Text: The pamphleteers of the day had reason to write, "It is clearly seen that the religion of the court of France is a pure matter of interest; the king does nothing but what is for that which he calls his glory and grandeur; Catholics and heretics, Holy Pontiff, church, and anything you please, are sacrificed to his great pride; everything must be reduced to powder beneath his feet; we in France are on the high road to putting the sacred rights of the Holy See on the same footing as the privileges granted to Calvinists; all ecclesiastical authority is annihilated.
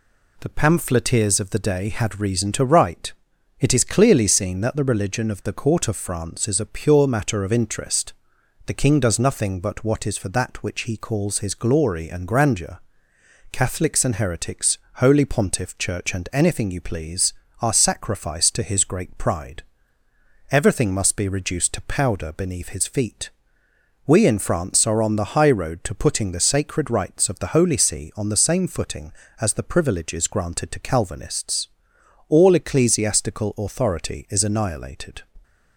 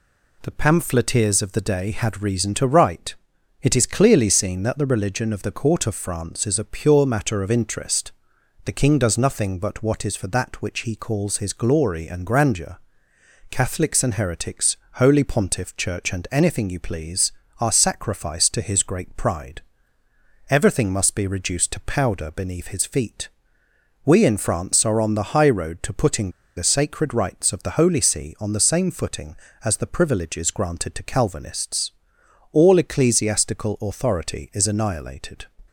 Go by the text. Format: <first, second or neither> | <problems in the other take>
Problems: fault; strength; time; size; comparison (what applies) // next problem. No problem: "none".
first | pauses between "putting" and "the"; slight; at 26.2 s; 0.27 s long